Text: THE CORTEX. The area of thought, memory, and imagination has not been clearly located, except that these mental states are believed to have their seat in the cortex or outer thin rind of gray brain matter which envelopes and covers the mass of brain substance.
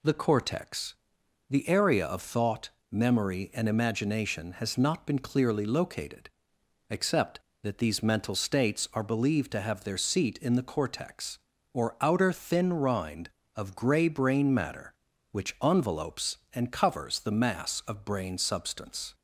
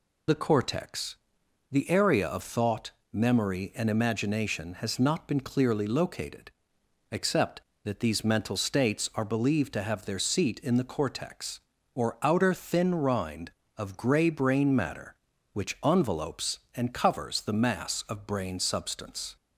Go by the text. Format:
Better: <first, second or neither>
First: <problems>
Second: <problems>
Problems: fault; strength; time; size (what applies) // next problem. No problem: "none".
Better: first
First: none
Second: loses the start of "THE"; at 0.2 s; 45 ms